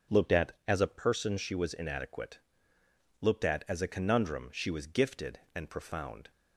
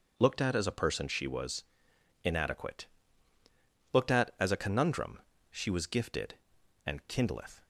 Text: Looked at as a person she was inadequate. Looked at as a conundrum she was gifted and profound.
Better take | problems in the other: first | pauses between "was" and "inadequate"; noticeable; at 1.6 s; 0.60 s long // pauses between "conundrum" and "she"; slight; at 5.1 s; 0.30 s long // says "kindleth" for "profound"; at 7.0 s

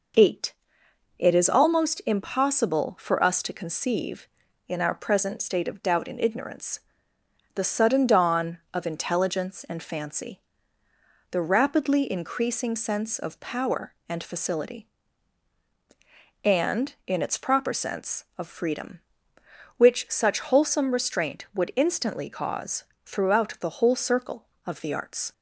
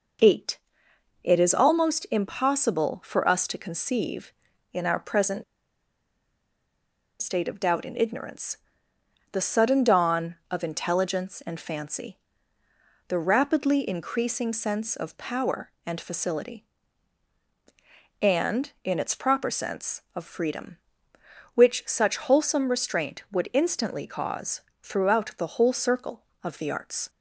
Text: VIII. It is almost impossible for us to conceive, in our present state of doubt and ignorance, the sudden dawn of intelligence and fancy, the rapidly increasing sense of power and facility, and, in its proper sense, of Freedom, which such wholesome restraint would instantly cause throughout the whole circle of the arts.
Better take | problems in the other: first | pauses between "present" and "state"; strong; at 5.4 s; 1.7 s long // pauses between "cause" and "throughout"; slight; at 24.5 s; 0.22 s long; slight in the first

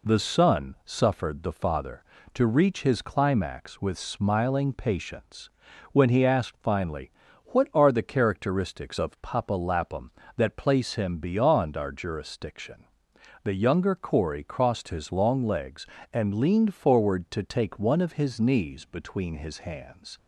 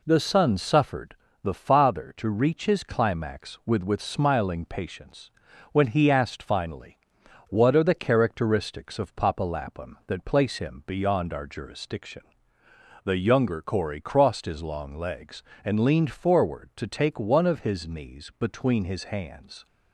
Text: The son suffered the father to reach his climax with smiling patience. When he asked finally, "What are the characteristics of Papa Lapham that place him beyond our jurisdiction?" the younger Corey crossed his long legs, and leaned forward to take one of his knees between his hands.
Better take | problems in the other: first | pauses between "suffered" and "the"; slight; at 1.1 s; 0.30 s long // says "with" twice; at 3.8 s

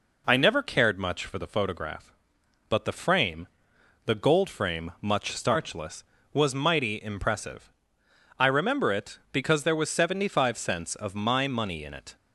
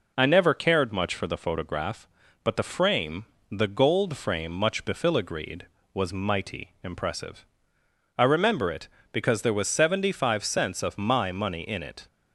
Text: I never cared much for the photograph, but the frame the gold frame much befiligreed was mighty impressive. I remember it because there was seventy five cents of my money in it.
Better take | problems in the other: second | pauses between "frame" and "the"; noticeable; at 3.4 s; 0.58 s long; slight in the second // says "starchless" for "befiligreed"; at 5.3 s

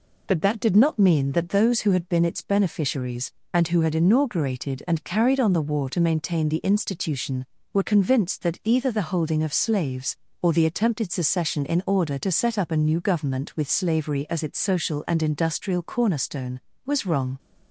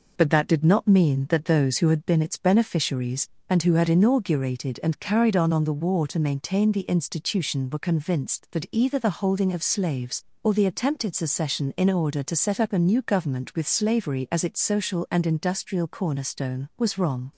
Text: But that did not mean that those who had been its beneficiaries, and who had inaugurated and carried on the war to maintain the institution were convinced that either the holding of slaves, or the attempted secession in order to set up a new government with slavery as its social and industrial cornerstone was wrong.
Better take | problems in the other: first | says "on" twice; at 5.5 s

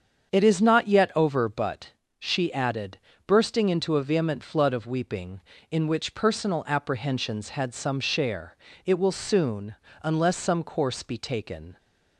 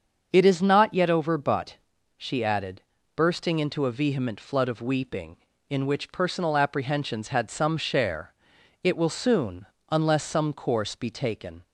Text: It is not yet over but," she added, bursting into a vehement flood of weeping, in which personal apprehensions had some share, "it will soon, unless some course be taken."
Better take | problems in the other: neither | starts louder than the rest; the same in both

